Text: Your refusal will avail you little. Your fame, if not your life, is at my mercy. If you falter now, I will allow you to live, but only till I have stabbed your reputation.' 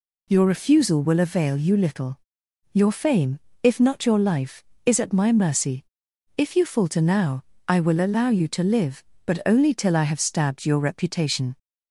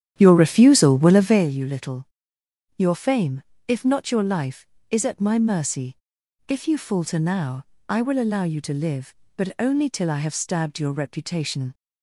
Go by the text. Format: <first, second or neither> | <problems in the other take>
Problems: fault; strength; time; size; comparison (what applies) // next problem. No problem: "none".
first | starts louder than the rest; strong; until 1.5 s; 10 dB